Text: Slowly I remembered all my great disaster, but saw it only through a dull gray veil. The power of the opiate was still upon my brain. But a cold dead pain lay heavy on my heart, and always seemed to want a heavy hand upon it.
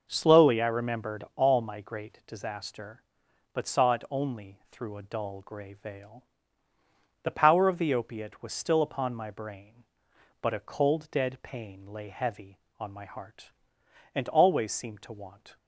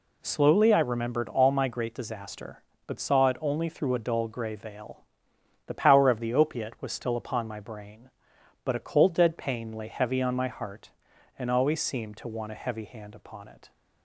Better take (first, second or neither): second